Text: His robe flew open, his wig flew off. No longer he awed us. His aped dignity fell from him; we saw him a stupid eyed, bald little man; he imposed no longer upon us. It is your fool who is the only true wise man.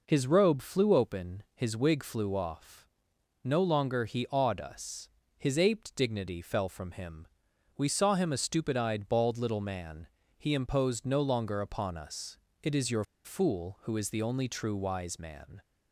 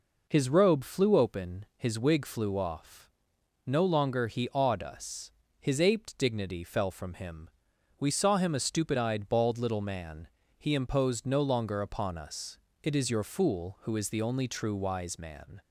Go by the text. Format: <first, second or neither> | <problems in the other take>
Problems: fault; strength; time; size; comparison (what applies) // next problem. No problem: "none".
second | pauses between "your" and "fool"; slight; at 13.0 s; 0.21 s long